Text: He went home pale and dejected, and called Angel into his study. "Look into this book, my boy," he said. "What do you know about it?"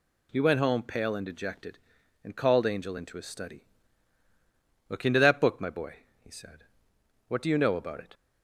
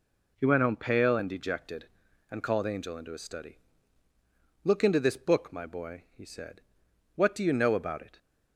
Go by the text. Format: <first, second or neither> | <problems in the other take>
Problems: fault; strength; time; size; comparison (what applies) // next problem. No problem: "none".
second | says "that" for "this"; at 5.1 s